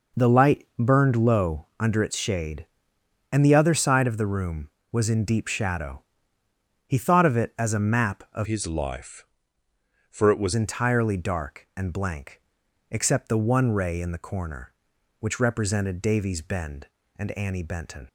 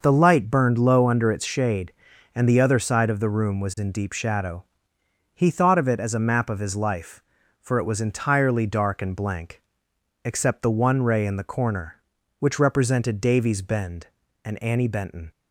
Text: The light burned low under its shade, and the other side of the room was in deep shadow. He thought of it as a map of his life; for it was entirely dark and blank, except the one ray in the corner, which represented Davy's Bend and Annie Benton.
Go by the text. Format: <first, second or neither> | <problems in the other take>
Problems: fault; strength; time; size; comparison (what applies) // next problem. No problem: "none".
second | changes voice from "his" to "was"; from 8.4 to 10.5 s; 2.1 s long